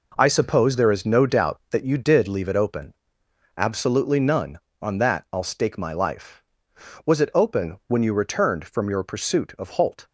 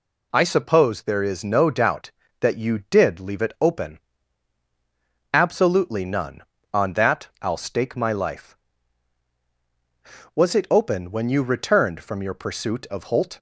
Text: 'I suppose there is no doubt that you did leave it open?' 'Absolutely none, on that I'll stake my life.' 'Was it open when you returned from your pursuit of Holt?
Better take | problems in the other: second | gets quieter; strong; throughout; 9 dB

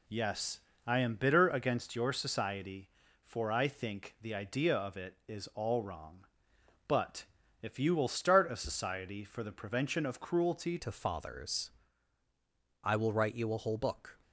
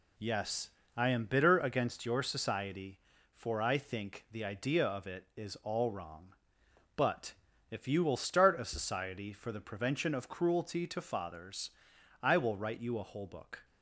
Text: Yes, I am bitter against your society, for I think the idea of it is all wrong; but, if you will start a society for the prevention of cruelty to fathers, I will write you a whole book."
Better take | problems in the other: second | changes voice at "to"; from 10.7 s on; 3.4 s long

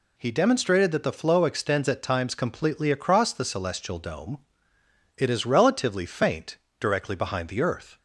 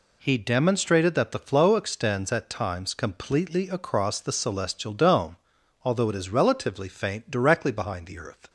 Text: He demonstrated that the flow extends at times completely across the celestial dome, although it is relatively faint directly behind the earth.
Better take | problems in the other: second | skips "although"; at 4.7 s // pauses between "faint" and "directly"; slight; at 6.5 s; 0.22 s long

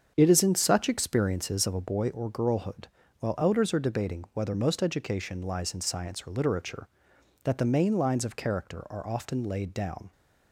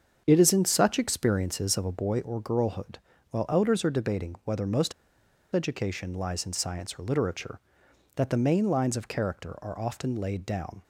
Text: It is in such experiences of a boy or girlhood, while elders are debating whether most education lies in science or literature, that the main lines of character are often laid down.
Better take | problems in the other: first | starts louder than the rest; strong; until 1.2 s; 7.5 dB; strong in the first // pauses between "most" and "education"; noticeable; at 4.9 s; 0.62 s long

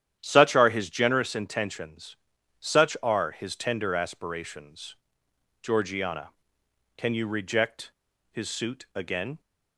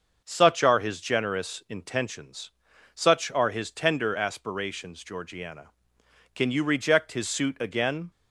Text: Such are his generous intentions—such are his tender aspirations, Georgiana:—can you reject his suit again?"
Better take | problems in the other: second | starts louder than the rest; strong; until 1.2 s; 10.5 dB; also in the second // pauses between "reject" and "his"; at 7.9 s; 0.37 s long

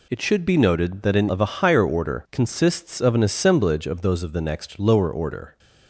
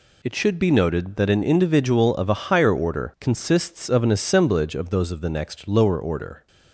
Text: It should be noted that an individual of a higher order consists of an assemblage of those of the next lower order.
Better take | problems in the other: second | skips "individual"; at 1.2 s

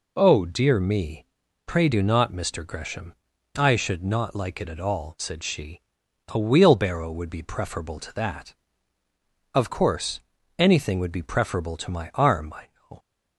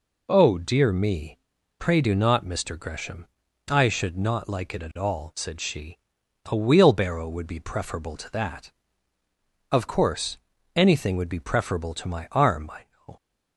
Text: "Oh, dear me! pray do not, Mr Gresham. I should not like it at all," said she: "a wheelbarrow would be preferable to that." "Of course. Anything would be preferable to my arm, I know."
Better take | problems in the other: neither | none

